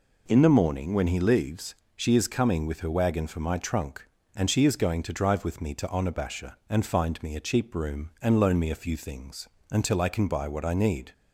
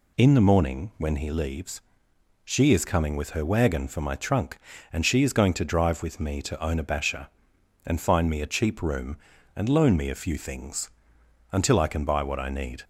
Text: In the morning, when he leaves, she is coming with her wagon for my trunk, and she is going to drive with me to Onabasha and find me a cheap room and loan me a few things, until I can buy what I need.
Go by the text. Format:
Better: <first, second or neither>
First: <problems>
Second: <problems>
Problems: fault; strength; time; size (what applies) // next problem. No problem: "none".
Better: neither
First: none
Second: none